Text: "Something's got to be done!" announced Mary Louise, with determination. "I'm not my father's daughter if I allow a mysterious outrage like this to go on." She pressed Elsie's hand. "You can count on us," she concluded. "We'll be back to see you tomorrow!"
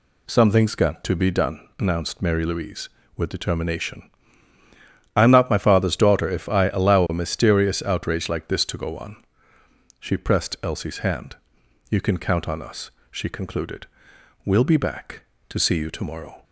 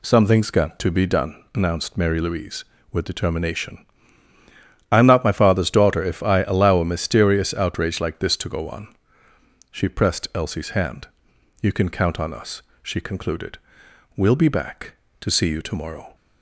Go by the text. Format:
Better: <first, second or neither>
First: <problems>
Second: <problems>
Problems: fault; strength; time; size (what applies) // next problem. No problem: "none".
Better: neither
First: none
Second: none